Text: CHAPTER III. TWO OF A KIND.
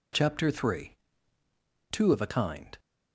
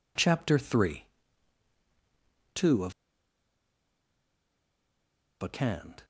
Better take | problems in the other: first | pauses between "OF" and "A"; strong; at 2.9 s; 2.4 s long

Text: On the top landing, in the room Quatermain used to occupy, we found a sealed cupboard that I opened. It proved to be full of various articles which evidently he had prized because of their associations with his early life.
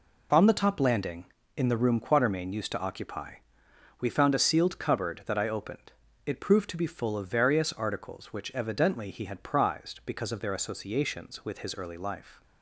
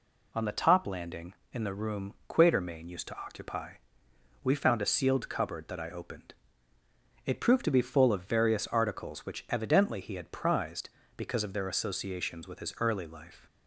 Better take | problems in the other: neither | none

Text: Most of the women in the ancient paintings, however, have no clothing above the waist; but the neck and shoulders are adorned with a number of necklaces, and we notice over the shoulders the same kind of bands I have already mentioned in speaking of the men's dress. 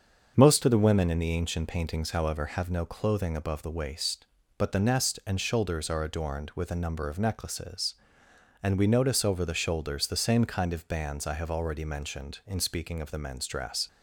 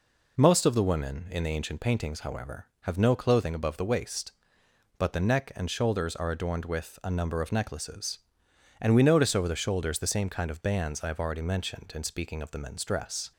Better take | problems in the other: second | starts louder than the rest; until 1.3 s; 6.5 dB // says "nest" for "neck"; at 4.8 s

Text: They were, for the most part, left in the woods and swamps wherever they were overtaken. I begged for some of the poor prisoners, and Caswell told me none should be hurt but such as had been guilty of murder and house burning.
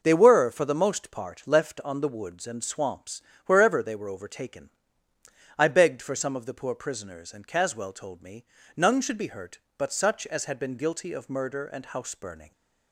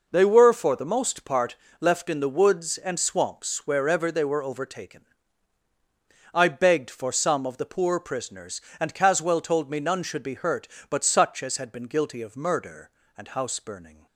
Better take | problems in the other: second | says "on" for "in"; at 1.8 s // pauses between "swamps" and "wherever"; slight; at 3.2 s; 0.24 s long // pauses between "me" and "none"; slight; at 8.4 s; 0.30 s long

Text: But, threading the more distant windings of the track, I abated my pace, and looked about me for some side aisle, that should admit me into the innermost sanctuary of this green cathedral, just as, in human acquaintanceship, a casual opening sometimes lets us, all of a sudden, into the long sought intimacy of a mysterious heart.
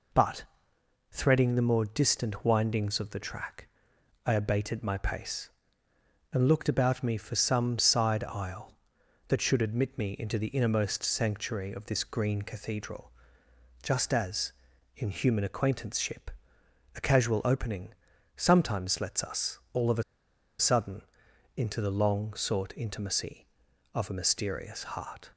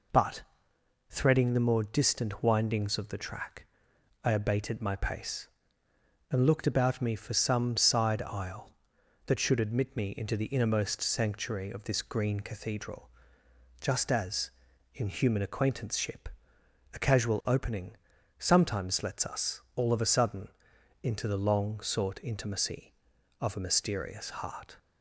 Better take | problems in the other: second | pauses between "opening" and "sometimes"; at 17.9 s; 0.42 s long; also in the second // pauses between "a" and "sudden"; noticeable; at 20.0 s; 0.56 s long

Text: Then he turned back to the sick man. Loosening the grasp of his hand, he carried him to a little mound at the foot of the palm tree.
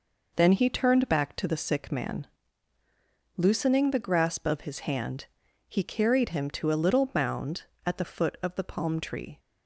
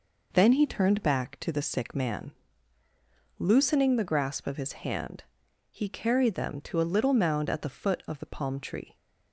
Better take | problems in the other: first | says "them" for "him"; at 6.3 s

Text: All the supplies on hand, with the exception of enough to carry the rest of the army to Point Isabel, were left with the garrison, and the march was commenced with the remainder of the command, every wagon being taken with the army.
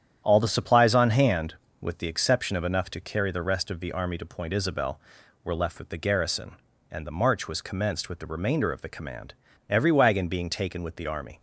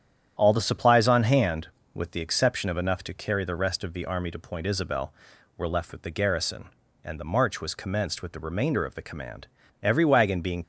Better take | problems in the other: first | starts louder than the rest; strong; until 1.3 s; 9.5 dB; strong in the first // stops before "taken with the army"; at 10.6 s

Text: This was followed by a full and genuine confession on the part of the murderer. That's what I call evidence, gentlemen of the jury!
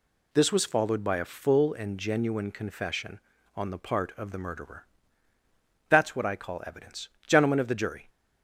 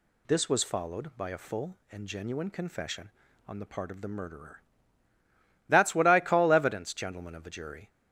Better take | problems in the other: neither | none

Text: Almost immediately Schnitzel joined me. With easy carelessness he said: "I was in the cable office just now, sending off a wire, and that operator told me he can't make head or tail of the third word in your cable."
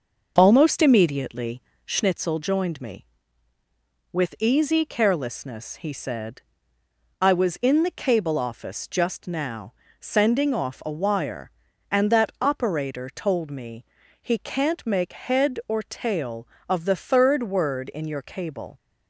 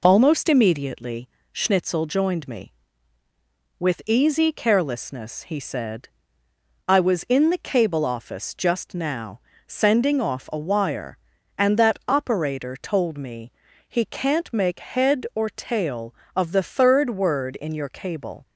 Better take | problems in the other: second | starts louder than the rest; until 2.1 s; 6 dB // pauses between "immediately" and "Schnitzel"; slight; at 1.6 s; 0.24 s long; slight in the second // pauses between "me" and "he"; at 13.8 s; 0.38 s long; also in the second

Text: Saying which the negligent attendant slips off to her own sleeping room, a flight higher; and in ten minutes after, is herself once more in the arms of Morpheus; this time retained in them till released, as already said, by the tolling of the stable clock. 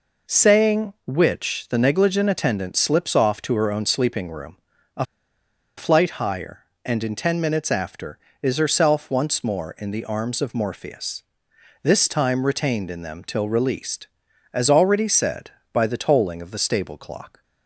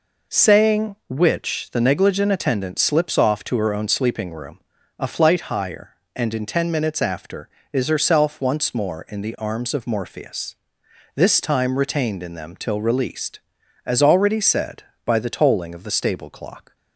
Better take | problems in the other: second | pauses between "a" and "flight"; noticeable; at 5.0 s; 0.72 s long

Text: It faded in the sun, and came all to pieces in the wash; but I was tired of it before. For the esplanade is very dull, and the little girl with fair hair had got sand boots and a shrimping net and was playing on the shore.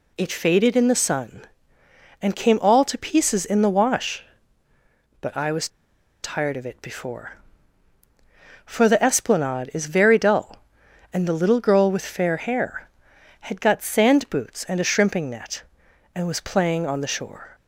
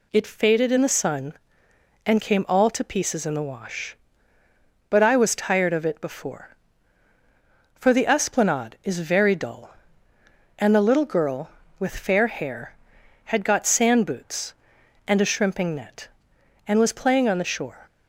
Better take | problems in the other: second | pauses between "was" and "tired"; noticeable; at 5.6 s; 0.55 s long

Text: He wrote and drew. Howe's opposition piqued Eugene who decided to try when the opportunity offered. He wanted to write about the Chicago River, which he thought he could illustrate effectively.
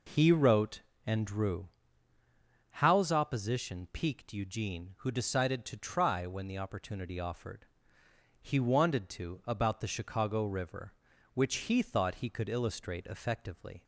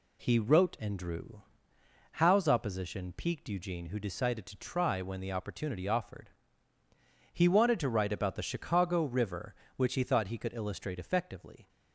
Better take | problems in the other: second | skips "write"; at 9.4 s

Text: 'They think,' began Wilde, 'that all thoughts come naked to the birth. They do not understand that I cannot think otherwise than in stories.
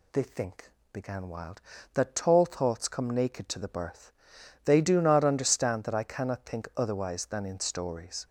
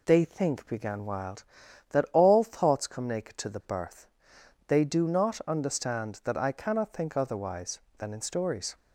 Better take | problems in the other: second | says "tall" for "all"; at 2.1 s

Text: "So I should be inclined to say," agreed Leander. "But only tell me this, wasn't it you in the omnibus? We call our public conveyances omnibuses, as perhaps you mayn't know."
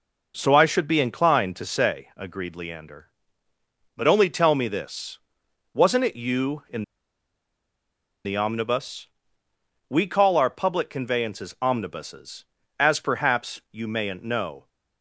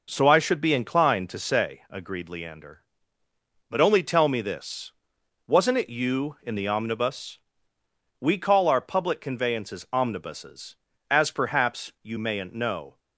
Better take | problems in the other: second | pauses between "in" and "the"; strong; at 6.8 s; 1.4 s long

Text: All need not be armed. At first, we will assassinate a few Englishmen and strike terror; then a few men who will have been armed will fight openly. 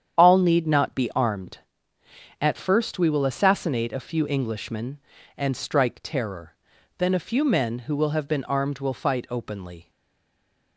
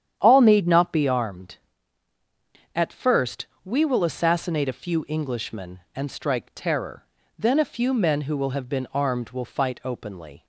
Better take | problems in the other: second | starts louder than the rest; strong; until 1.2 s; 8.5 dB; strong in the second // stays silent after the last word; slight; from 9.8 s on; 0.9 s long

